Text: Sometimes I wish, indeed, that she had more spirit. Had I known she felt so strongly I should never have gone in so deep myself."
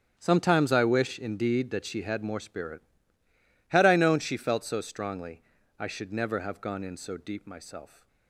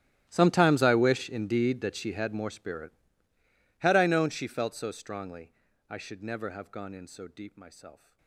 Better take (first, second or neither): first